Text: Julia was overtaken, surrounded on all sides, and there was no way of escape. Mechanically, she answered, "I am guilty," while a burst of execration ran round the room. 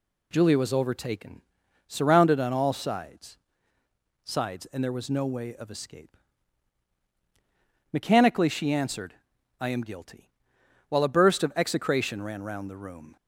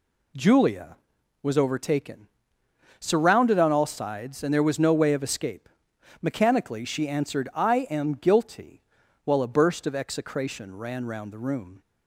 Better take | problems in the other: second | says "sides" twice; at 4.2 s

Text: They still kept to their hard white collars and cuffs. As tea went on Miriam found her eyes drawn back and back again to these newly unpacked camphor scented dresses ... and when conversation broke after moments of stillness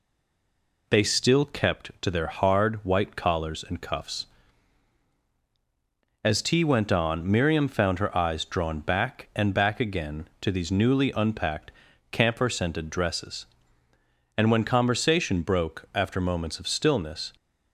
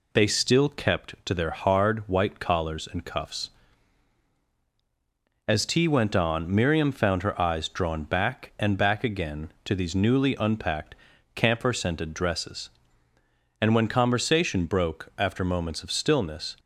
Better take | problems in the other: second | stays silent before the first word; slight; until 0.8 s; 0.8 s long // pauses between "unpacked" and "camphor"; at 11.7 s; 0.40 s long; also in the second

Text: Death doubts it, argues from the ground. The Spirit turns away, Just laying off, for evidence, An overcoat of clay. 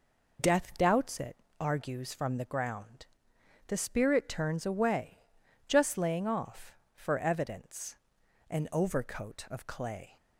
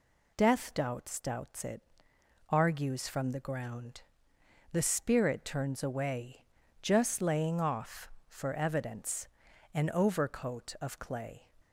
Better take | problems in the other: first | says "doubts" twice; at 1.1 s

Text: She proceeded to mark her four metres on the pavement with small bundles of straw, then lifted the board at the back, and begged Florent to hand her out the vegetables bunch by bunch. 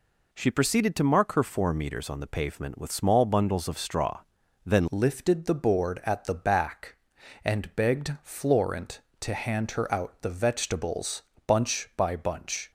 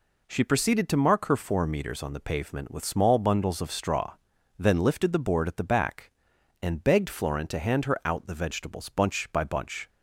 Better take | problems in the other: second | changes voice at "lifted"; from 4.9 s on; 7.8 s long // pauses between "vegetables" and "bunch"; slight; at 11.2 s; 0.24 s long

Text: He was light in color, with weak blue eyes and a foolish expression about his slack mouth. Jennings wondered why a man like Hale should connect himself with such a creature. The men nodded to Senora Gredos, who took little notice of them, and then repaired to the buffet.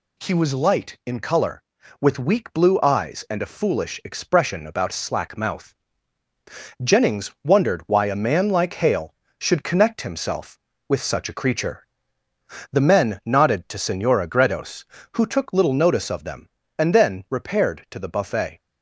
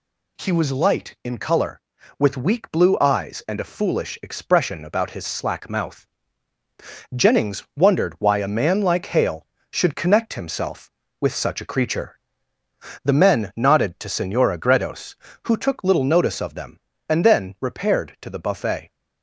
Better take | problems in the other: second | skips "his"; at 4.9 s

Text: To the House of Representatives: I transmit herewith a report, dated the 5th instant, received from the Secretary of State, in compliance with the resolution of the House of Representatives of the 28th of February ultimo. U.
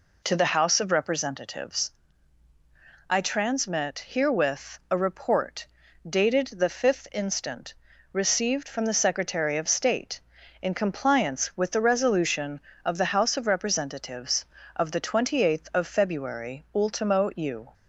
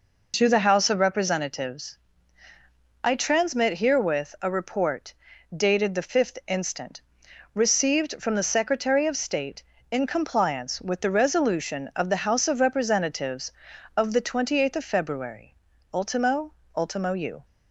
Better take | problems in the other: first | pauses between "February" and "ultimo"; at 15.5 s; 0.38 s long // says "ultimo" twice; at 16.7 s

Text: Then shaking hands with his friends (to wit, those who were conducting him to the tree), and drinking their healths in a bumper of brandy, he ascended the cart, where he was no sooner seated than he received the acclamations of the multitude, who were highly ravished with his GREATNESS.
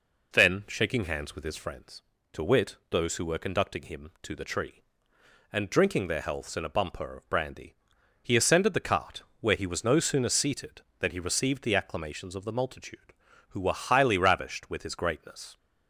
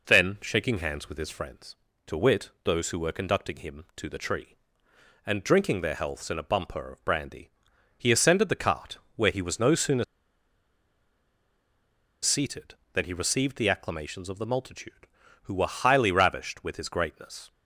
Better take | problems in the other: first | pauses between "sooner" and "seated"; strong; at 10.0 s; 2.1 s long

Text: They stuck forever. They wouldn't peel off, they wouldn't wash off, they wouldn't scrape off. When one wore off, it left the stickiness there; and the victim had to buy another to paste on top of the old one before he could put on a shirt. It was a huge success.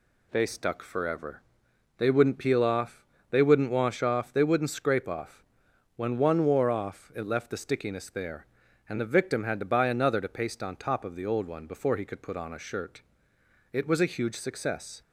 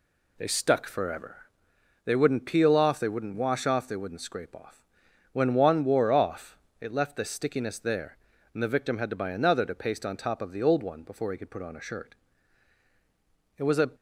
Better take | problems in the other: first | stops before "huge success"; at 13.9 s

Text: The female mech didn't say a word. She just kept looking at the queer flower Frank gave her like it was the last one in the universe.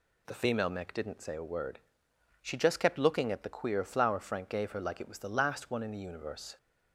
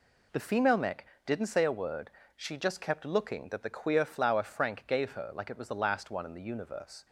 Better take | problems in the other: first | pauses between "mech" and "didn't"; slight; at 1.0 s; 0.18 s long // says "that" for "at"; at 3.4 s

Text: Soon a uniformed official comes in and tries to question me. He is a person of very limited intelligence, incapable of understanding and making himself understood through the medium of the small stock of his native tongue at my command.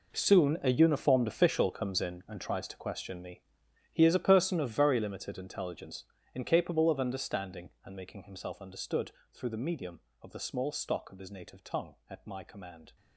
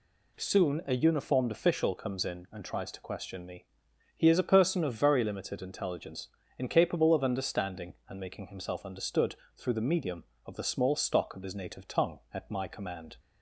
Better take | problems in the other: second | gets quieter; strong; throughout; 14 dB // pauses between "understood" and "through"; slight; at 9.1 s; 0.20 s long; slight in the second

